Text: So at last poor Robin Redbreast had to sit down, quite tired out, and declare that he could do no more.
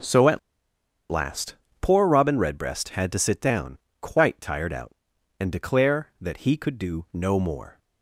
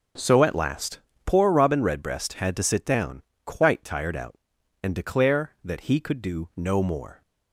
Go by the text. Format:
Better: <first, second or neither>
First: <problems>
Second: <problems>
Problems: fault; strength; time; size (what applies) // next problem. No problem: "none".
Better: second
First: starts louder than the rest; until 2.0 s; 6.5 dB // pauses between "at" and "last"; noticeable; at 0.3 s; 0.71 s long // pauses between "last" and "poor"; slight; at 1.5 s; 0.26 s long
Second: starts louder than the rest; until 1.4 s; 6.5 dB // pauses between "last" and "poor"; slight; at 0.9 s; 0.26 s long